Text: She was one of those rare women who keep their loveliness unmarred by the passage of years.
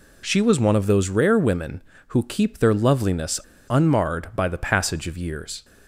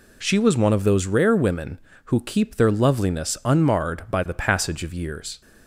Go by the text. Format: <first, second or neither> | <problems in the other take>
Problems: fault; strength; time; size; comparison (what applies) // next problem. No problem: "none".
second | pauses between "loveliness" and "unmarred"; slight; at 3.3 s; 0.30 s long